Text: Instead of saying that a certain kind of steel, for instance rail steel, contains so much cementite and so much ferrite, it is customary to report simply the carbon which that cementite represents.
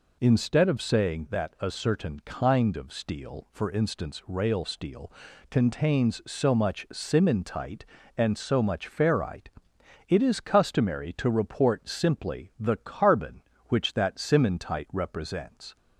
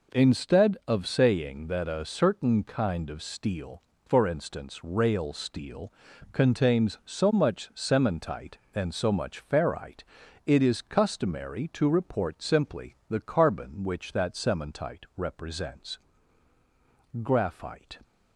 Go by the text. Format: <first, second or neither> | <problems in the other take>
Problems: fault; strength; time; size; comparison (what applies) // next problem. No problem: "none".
first | goes on to say "Graphite"; noticeable; from 17.2 s on; 0.78 s long